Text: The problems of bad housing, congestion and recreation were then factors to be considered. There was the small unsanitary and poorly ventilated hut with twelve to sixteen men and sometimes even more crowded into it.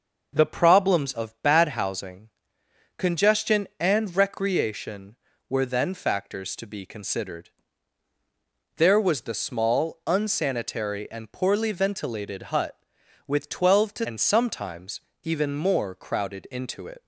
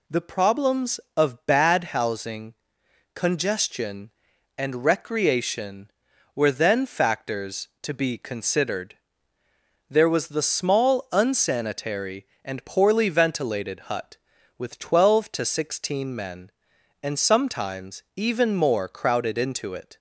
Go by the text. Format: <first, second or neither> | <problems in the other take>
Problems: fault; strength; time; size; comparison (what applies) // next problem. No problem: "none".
second | starts louder than the rest; until 1.3 s; 6 dB // skips "sixteen men"; at 14.0 s // pauses between "sometimes" and "even"; slight; at 14.9 s; 0.24 s long